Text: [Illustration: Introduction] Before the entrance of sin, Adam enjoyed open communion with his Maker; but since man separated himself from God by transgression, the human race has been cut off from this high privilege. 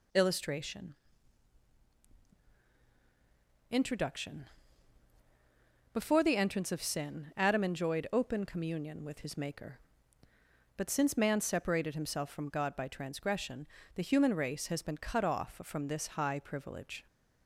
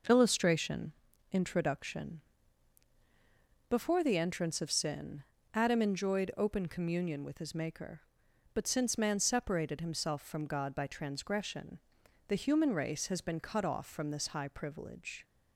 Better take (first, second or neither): first